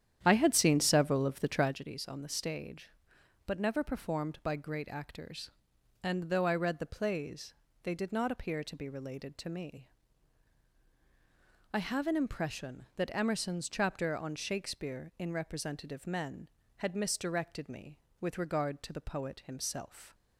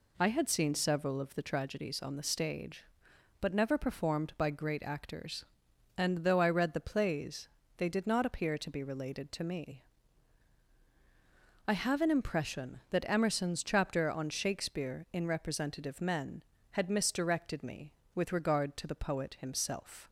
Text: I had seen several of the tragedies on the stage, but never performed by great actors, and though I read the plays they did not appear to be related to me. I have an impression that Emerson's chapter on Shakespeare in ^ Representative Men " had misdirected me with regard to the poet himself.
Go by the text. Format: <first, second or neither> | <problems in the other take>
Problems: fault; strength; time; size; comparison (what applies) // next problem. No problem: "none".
second | starts louder than the rest; strong; until 1.8 s; 10 dB // pauses between "plays" and "they"; slight; at 7.5 s; 0.28 s long; slight in the second